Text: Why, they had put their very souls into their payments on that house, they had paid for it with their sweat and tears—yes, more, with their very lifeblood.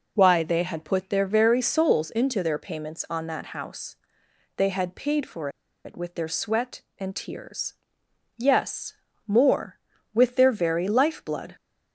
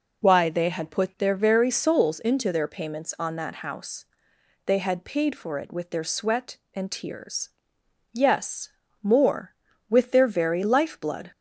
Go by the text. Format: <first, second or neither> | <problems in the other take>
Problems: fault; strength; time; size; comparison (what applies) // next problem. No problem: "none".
second | pauses between "for" and "it"; slight; at 5.5 s; 0.34 s long